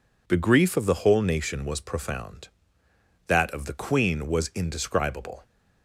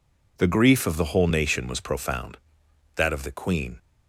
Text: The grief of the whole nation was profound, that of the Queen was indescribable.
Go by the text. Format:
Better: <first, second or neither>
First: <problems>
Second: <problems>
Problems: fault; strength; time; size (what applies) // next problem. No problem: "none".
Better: first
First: none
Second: stops before "was indescribable"; at 3.7 s